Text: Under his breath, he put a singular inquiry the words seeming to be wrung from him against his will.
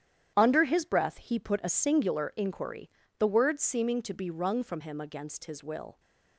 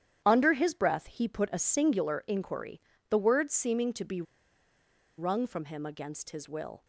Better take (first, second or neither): first